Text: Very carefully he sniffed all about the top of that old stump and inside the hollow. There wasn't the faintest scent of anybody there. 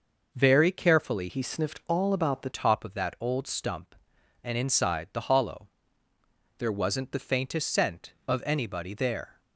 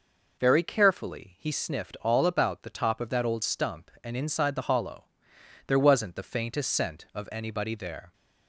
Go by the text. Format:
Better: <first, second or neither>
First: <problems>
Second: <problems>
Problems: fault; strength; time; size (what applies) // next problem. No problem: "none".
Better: second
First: changes voice from "he" to "the"; from 1.2 to 2.5 s; 1.3 s long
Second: none